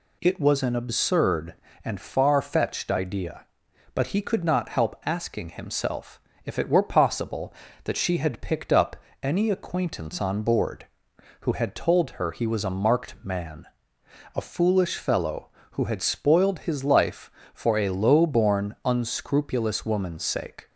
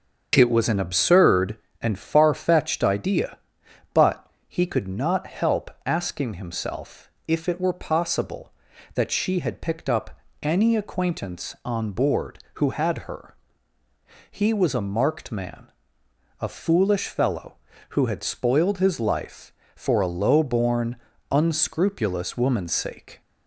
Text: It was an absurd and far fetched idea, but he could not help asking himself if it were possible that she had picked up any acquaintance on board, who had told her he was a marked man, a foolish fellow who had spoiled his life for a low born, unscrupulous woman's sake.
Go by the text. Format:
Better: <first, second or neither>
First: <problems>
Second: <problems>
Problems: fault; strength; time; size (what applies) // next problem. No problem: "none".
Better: first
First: pauses between "himself" and "if"; slight; at 6.1 s; 0.26 s long // pauses between "up" and "any"; slight; at 8.9 s; 0.26 s long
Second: starts louder than the rest; until 1.3 s; 7 dB // pauses between "but" and "he"; slight; at 4.2 s; 0.22 s long // pauses between "help" and "asking"; slight; at 5.7 s; 0.16 s long // pauses between "himself" and "if"; slight; at 7.0 s; 0.20 s long // pauses between "up" and "any"; slight; at 10.1 s; 0.24 s long // skips "told"; at 13.0 s // pauses between "her" and "he"; noticeable; at 13.3 s; 0.96 s long